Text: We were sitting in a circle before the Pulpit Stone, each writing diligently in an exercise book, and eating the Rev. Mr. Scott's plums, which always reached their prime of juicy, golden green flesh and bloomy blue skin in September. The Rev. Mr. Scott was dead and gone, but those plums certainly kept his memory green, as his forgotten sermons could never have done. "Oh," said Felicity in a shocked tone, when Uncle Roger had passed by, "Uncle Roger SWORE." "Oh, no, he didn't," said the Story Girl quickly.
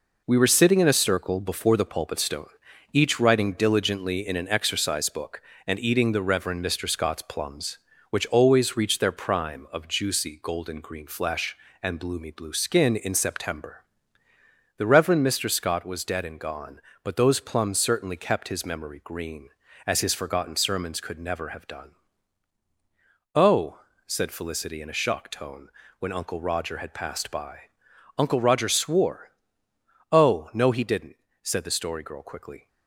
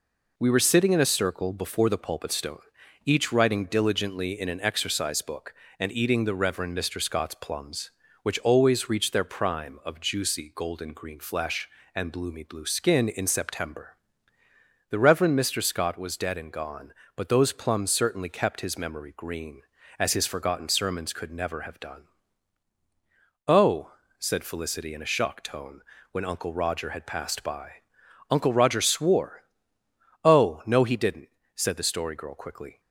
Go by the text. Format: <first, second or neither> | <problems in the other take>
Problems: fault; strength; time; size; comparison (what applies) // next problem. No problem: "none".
second | gets quieter; noticeable; throughout; 6 dB